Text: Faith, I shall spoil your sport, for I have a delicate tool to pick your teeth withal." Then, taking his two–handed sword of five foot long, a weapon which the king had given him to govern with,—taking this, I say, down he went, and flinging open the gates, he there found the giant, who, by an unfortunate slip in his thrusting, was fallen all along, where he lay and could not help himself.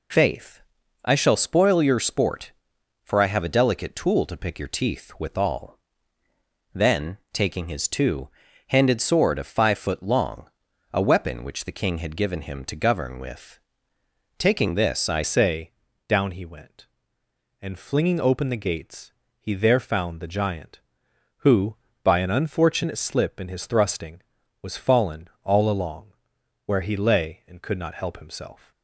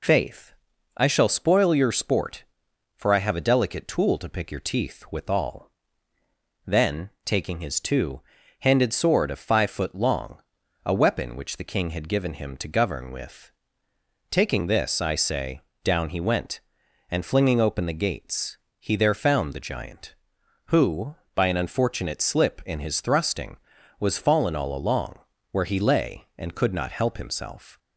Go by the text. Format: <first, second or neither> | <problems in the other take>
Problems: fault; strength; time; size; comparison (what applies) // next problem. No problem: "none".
second | changes voice at "say"; from 15.2 s on; 13.5 s long // pauses between "fallen" and "all"; slight; at 25.2 s; 0.16 s long